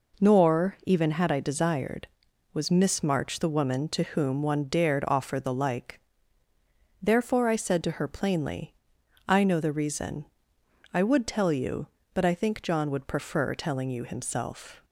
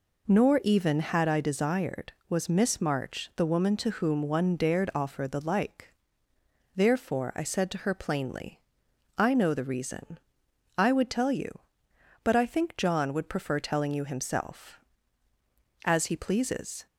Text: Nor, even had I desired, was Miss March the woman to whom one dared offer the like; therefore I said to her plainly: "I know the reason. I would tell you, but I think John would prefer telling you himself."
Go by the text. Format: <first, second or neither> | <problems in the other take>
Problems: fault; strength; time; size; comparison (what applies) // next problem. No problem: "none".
first | goes on to say "As he pleases"; noticeable; from 15.8 s on; 1.0 s long